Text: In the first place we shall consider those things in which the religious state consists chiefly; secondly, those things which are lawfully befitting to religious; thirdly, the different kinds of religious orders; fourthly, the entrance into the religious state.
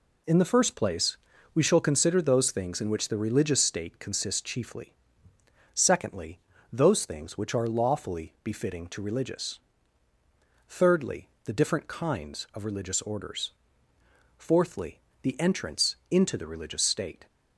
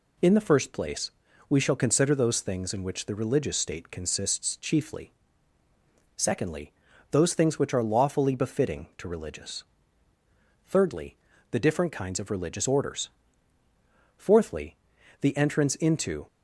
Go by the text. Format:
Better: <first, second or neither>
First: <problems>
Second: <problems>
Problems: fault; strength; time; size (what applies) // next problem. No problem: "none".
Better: first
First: pauses between "place" and "we"; slight; at 1.1 s; 0.36 s long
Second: pauses between "place" and "we"; at 1.1 s; 0.38 s long // stops before "the religious state"; at 16.2 s